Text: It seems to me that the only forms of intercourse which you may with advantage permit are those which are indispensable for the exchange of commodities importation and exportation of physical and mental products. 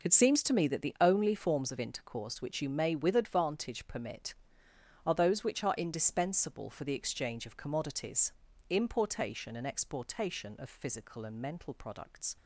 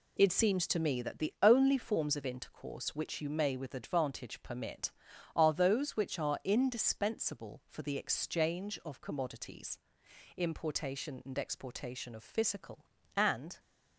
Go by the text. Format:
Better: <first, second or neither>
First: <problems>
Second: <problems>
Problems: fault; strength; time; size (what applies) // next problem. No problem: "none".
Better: first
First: pauses between "commodities" and "importation"; slight; at 8.3 s; 0.36 s long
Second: pauses between "commodities" and "importation"; noticeable; at 9.7 s; 0.58 s long // stops before "mental products"; at 13.5 s